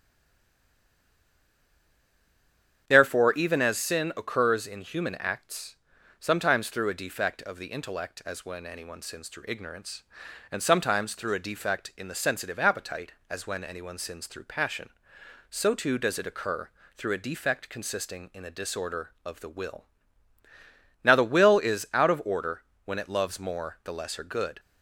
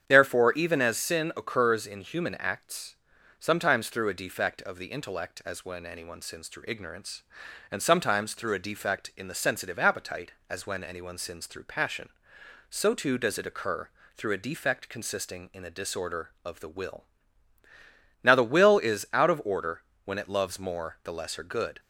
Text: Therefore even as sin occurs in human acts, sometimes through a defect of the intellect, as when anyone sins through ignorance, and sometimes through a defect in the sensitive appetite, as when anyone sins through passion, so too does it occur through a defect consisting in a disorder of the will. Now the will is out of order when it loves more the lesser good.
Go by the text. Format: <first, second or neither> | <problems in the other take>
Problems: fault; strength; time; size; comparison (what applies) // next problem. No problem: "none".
second | stays silent before the first word; strong; until 2.8 s; 2.8 s long // starts louder than the rest; strong; until 3.8 s; 8.5 dB; strong in the second // pauses between "occur" and "through"; slight; at 16.6 s; 0.28 s long; slight in the second // pauses between "order" and "when"; slight; at 22.6 s; 0.24 s long; slight in the second